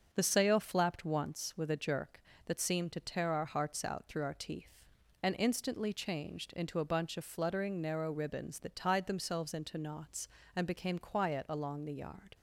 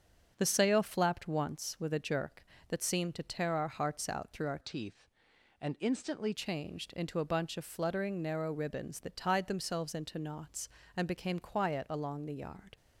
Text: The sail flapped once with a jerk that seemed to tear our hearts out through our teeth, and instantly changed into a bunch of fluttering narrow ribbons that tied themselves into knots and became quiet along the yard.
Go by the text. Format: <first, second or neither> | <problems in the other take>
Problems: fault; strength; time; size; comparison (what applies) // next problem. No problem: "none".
first | starts louder than the rest; strong; until 1.3 s; 7.5 dB; also in the first // changes voice from "teeth" to "instantly"; from 4.6 to 6.3 s; 1.7 s long